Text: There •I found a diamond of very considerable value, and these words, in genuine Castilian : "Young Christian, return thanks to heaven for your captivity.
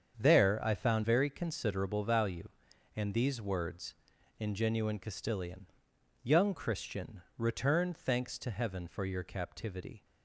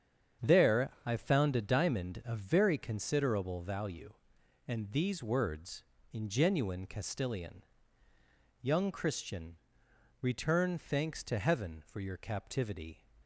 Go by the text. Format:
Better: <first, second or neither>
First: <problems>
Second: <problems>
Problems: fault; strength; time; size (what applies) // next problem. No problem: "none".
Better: second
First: starts louder than the rest; strong; until 1.2 s; 7.5 dB // skips "a diamond of"; at 1.0 s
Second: starts louder than the rest; strong; until 1.5 s; 8 dB